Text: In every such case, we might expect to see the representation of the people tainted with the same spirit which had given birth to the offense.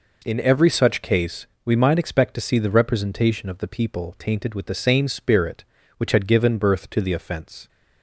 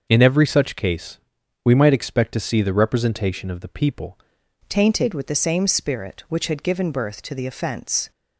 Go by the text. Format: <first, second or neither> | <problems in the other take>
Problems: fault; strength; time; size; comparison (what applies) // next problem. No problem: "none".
first | starts louder than the rest; until 1.1 s; 6.5 dB // changes voice at "tainted"; from 4.6 s on; 3.5 s long